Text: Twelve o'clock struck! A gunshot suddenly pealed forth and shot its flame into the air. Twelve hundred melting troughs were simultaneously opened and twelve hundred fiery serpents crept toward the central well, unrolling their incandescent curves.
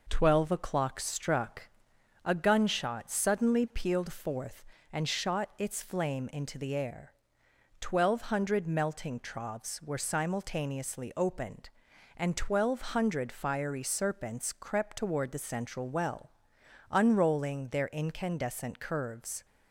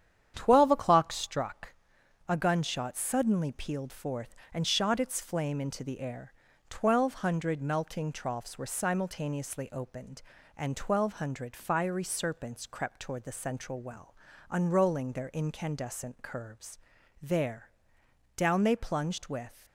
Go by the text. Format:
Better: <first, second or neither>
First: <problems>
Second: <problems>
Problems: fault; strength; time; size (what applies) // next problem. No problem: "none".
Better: first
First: none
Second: starts louder than the rest; strong; until 1.3 s; 9 dB // goes on to say "There down they plunged with"; strong; from 17.2 s on; 2.4 s long